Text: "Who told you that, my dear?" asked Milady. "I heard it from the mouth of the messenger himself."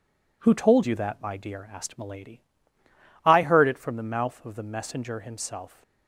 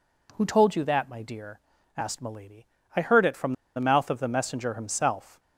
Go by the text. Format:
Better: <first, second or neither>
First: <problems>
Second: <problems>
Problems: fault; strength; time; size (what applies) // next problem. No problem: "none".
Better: first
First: none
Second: pauses between "from" and "the"; slight; at 3.5 s; 0.23 s long